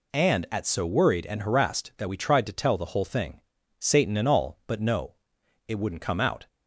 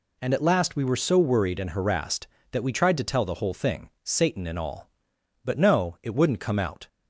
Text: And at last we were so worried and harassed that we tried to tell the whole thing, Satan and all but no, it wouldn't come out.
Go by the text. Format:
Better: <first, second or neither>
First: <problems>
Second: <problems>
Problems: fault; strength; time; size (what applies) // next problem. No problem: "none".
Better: second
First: skips "last we were"; at 0.6 s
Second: none